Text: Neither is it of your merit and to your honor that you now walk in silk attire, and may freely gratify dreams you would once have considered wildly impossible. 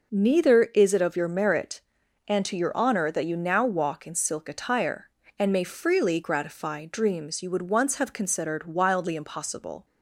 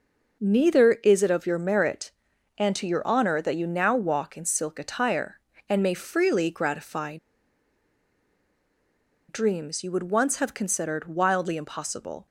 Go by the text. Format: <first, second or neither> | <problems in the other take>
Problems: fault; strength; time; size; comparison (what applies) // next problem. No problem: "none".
first | pauses between "gratify" and "dreams"; strong; at 7.1 s; 2.1 s long